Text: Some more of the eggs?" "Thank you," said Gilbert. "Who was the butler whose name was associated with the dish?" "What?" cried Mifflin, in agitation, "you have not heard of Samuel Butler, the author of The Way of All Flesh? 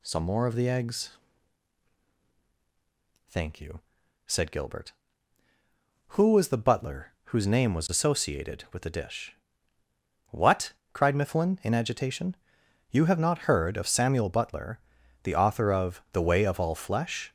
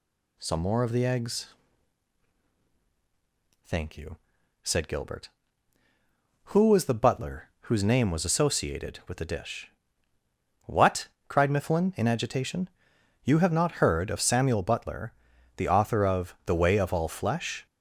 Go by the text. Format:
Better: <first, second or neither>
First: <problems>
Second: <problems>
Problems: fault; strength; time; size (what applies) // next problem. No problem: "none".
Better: neither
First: none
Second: none